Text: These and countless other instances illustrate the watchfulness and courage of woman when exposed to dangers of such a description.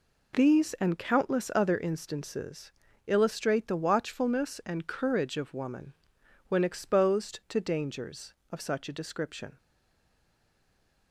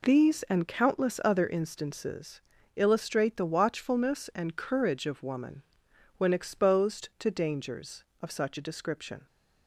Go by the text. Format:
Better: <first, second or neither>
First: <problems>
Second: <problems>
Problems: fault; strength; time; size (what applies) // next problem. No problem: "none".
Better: second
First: pauses between "instances" and "illustrate"; slight; at 2.7 s; 0.34 s long // pauses between "woman" and "when"; noticeable; at 5.9 s; 0.56 s long // stays silent after the last word; noticeable; from 9.5 s on; 1.6 s long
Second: pauses between "instances" and "illustrate"; slight; at 2.4 s; 0.34 s long // pauses between "woman" and "when"; noticeable; at 5.6 s; 0.56 s long